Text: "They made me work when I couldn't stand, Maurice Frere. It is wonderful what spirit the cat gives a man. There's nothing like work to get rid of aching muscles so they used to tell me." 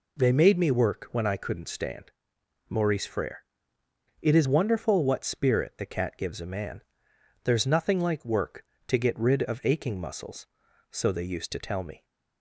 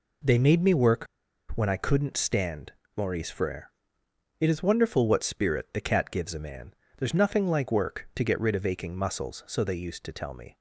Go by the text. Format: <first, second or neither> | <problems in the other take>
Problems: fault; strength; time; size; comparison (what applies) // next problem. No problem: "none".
first | pauses between "work" and "when"; noticeable; at 1.0 s; 0.48 s long